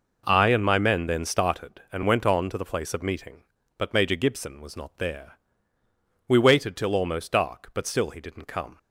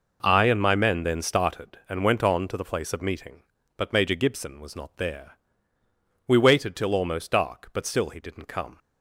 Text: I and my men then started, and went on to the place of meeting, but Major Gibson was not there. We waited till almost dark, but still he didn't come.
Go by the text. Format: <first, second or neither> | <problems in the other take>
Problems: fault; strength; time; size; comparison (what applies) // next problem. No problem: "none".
neither | none